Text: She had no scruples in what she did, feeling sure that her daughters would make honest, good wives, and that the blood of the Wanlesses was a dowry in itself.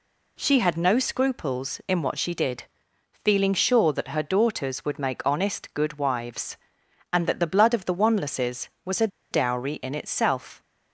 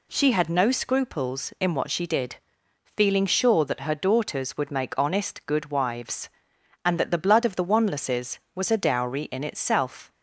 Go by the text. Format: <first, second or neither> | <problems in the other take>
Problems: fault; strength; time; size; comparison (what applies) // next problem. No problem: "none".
second | pauses between "a" and "dowry"; slight; at 9.0 s; 0.24 s long